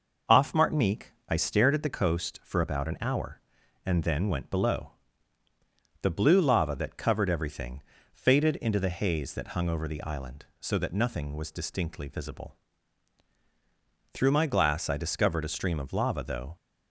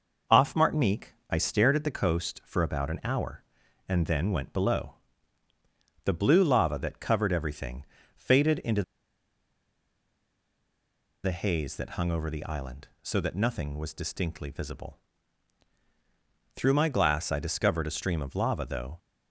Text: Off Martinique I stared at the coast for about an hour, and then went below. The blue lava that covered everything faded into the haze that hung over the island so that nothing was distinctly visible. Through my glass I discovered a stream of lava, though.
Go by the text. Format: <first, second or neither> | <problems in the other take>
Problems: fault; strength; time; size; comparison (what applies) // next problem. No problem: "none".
first | pauses between "Martinique" and "I"; slight; at 1.1 s; 0.16 s long; slight in the first // pauses between "everything" and "faded"; slight; at 7.8 s; 0.30 s long; slight in the first // pauses between "into" and "the"; strong; at 8.8 s; 2.4 s long